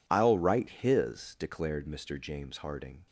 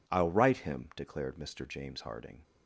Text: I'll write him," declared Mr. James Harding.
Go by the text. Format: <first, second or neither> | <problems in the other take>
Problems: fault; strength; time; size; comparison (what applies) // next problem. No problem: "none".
second | says "his" for "him"; at 0.6 s